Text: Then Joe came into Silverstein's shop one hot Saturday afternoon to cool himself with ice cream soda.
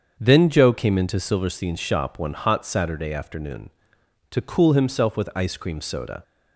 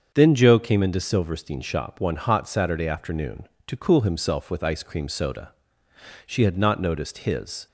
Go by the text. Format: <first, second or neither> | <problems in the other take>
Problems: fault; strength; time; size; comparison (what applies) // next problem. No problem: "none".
first | starts louder than the rest; until 1.1 s; 7 dB; also in the first // goes on to say "She had not noticed his"; from 6.2 s on; 1.4 s long